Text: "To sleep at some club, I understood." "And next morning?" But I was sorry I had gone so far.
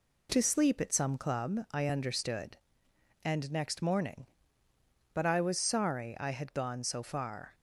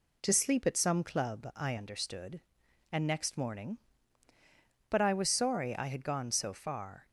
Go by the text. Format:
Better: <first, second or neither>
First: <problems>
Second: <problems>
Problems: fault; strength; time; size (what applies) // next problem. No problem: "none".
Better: neither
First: none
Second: none